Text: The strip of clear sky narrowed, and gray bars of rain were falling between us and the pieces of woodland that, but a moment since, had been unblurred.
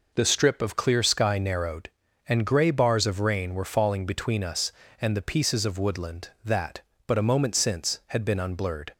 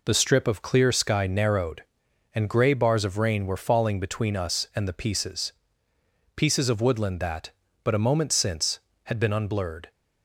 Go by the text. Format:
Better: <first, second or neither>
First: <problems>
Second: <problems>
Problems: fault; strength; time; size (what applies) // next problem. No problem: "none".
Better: first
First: none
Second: says "pieces" twice; at 6.3 s